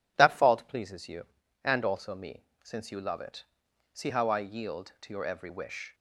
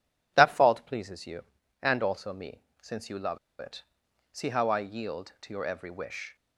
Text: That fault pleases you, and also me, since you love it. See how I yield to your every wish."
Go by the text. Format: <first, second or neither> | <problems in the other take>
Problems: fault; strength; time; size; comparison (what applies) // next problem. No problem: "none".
first | pauses between "love" and "it"; slight; at 3.3 s; 0.23 s long